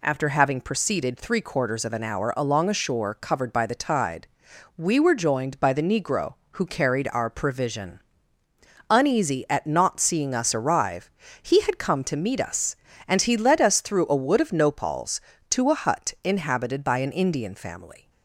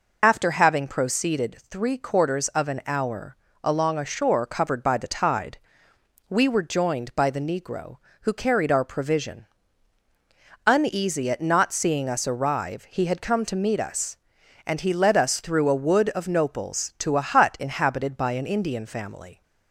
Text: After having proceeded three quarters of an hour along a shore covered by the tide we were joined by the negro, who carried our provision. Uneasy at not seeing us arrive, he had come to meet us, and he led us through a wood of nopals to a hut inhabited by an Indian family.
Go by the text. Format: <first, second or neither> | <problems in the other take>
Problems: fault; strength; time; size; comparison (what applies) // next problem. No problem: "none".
first | loses the start of "After"; at 0.2 s; 70 ms // pauses between "hour" and "along"; slight; at 3.3 s; 0.28 s long // pauses between "tide" and "we"; noticeable; at 5.5 s; 0.72 s long; noticeable in the first